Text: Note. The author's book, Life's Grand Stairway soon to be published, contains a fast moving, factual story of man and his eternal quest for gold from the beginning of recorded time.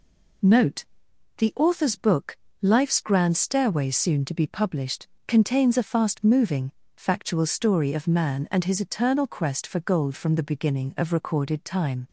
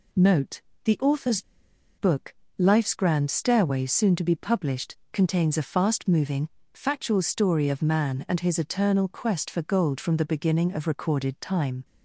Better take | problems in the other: first | pauses between "author's" and "book"; noticeable; at 1.4 s; 0.56 s long

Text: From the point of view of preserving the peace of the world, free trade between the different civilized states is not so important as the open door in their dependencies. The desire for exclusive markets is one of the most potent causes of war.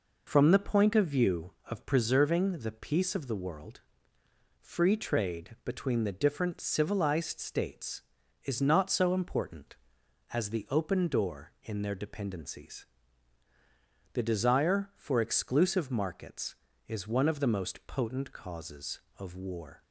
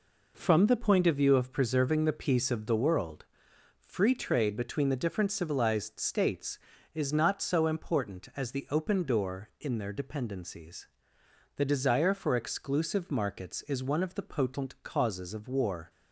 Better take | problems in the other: first | skips "most"; at 14.2 s

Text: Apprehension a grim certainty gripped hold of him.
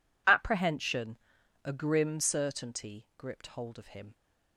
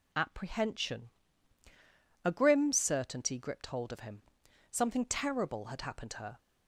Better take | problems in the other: first | pauses between "Apprehension" and "a"; at 1.0 s; 1.1 s long; also in the first // goes on to say "Something terrible had happened to her"; strong; from 4.6 s on; 1.6 s long

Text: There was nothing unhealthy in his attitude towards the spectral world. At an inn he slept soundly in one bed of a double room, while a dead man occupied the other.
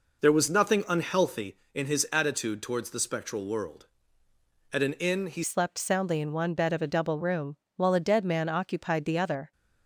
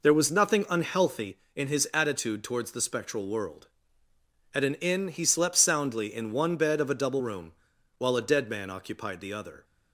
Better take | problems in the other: second | changes voice at "slept"; from 5.4 s on; 4.1 s long

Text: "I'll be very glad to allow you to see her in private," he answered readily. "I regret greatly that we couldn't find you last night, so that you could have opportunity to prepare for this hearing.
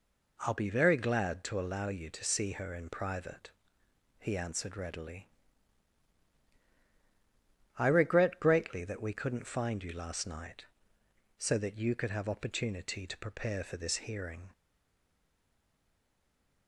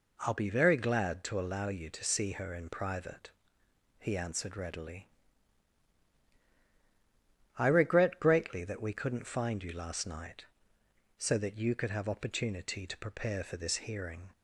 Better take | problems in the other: second | stays silent after the last word; from 14.5 s on; 2.1 s long

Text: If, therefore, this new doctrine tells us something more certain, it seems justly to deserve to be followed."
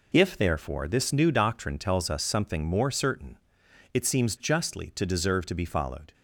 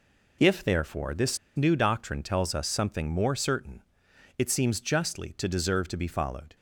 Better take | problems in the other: first | pauses between "this" and "new"; slight; at 1.3 s; 0.18 s long

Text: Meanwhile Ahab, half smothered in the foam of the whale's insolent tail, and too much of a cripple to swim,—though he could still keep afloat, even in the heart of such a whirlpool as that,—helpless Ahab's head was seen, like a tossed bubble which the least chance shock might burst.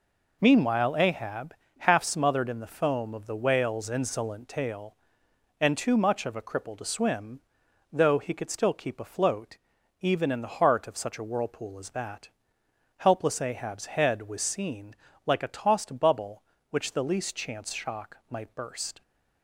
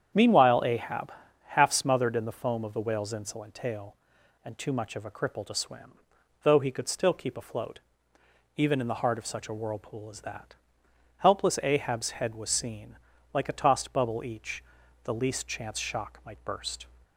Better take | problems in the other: first | starts louder than the rest; strong; until 1.5 s; 8.5 dB // says "each" for "which"; at 14.2 s

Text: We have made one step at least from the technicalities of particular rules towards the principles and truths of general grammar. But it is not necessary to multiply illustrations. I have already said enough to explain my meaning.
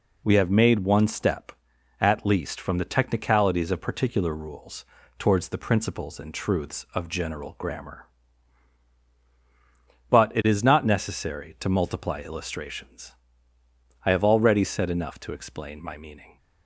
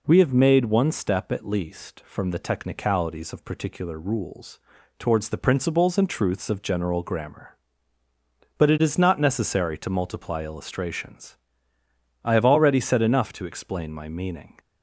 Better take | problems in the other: neither | pauses between "rules" and "towards"; the same in both

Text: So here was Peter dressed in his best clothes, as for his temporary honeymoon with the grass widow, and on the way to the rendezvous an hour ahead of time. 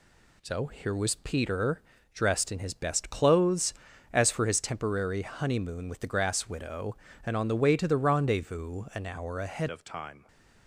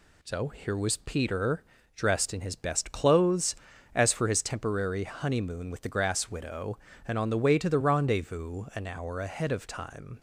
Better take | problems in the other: second | pauses between "Peter" and "dressed"; slight; at 1.8 s; 0.32 s long; slight in the second // changes voice at "of"; from 9.7 s on; 0.5 s long // stays silent after the last word; slight; from 10.1 s on; 0.5 s long

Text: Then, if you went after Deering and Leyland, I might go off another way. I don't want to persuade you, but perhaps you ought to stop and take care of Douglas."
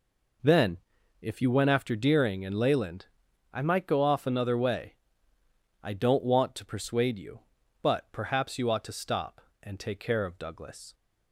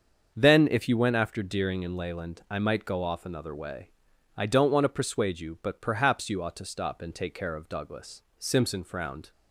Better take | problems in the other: first | starts louder than the rest; until 1.3 s; 7 dB // goes on to say "Simpson frowned"; noticeable; from 8.3 s on; 0.92 s long

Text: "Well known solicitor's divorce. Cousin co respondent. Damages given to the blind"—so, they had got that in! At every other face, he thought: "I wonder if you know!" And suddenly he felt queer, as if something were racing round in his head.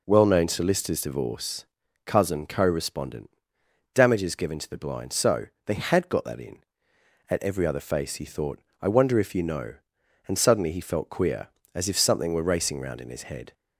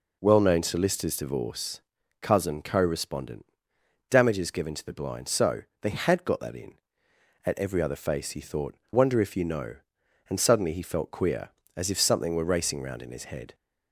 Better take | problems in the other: first | skips "I"; at 8.8 s

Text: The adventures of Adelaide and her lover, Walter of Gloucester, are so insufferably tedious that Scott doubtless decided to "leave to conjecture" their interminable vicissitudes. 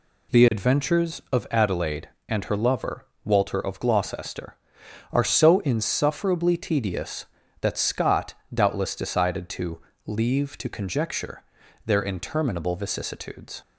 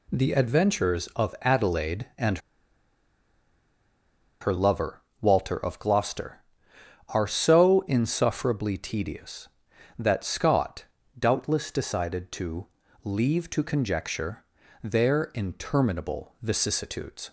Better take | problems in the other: first | pauses between "and" and "her"; strong; at 2.3 s; 2.0 s long // pauses between "Scott" and "doubtless"; slight; at 10.8 s; 0.34 s long; slight in the first // pauses between "to" and "leave"; at 12.6 s; 0.38 s long; slight in the first // pauses between "conjecture" and "their"; at 14.4 s; 0.38 s long; also in the first

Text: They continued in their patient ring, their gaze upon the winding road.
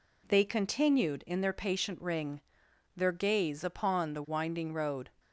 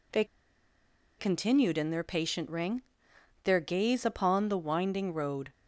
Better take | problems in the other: first | pauses between "They" and "continued"; noticeable; at 0.2 s; 0.94 s long

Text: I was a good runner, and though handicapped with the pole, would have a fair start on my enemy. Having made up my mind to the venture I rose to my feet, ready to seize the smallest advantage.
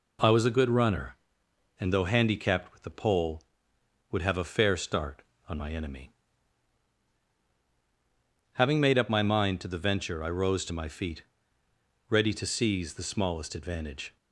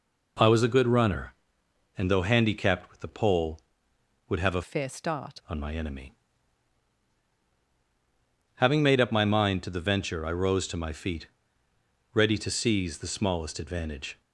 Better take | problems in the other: first | changes voice from "fair" to "start"; from 4.6 to 5.3 s; 0.7 s long

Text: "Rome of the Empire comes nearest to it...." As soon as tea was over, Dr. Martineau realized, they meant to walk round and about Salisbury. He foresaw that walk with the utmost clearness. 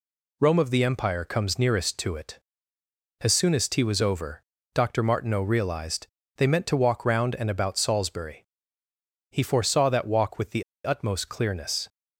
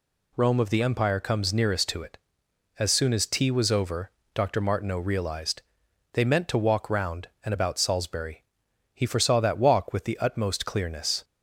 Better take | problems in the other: second | pauses between "the" and "utmost"; slight; at 10.6 s; 0.23 s long

